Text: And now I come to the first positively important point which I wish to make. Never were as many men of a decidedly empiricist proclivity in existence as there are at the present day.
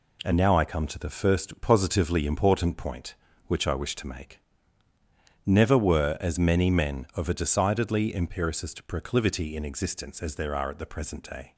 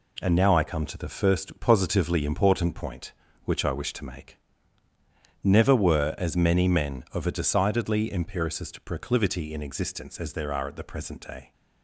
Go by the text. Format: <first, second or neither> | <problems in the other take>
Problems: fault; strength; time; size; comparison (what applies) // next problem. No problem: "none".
neither | none